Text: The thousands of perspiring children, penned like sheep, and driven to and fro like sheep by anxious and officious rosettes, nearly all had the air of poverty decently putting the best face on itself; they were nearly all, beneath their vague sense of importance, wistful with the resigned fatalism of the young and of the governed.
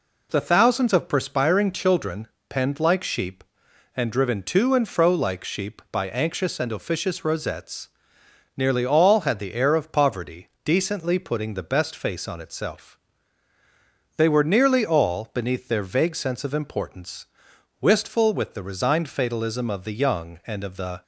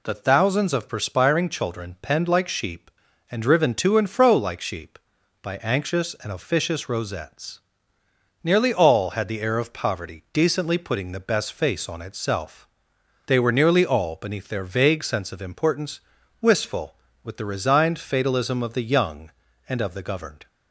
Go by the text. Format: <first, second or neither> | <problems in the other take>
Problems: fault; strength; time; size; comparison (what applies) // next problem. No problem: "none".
second | pauses between "poverty" and "decently"; slight; at 10.4 s; 0.16 s long // stops before "governed"; at 21.0 s